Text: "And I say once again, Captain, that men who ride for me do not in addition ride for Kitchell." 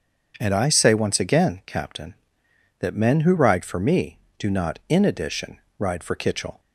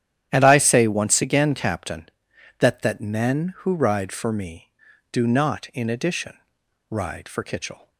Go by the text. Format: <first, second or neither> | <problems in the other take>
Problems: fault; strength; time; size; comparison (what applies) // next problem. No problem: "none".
first | starts louder than the rest; strong; until 1.3 s; 10.5 dB; also in the first // says "that" twice; at 2.8 s // pauses between "addition" and "ride"; noticeable; at 6.3 s; 0.51 s long; slight in the first